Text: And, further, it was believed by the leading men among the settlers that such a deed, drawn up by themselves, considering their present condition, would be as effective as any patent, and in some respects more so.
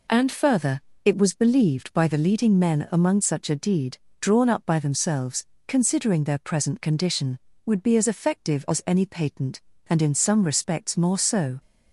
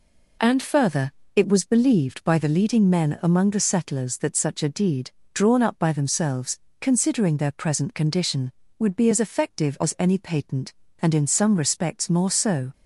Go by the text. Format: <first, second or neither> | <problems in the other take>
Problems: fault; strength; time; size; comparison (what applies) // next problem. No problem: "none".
second | skips "the settlers that"; at 3.2 s